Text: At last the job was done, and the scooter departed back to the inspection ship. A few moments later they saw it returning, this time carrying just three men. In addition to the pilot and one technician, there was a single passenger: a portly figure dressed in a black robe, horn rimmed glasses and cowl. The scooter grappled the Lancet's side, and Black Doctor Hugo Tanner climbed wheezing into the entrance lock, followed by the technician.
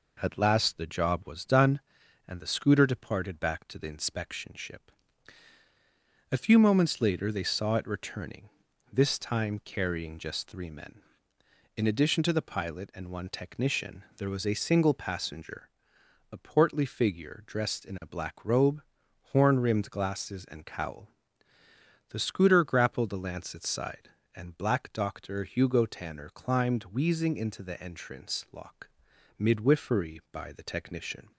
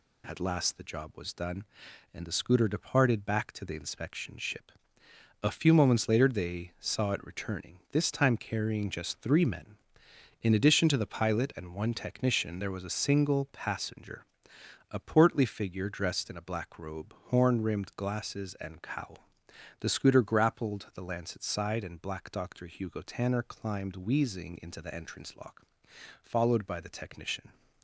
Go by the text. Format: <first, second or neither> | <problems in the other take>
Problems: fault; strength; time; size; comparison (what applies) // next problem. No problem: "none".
second | says "midwifery" for "followed"; at 29.3 s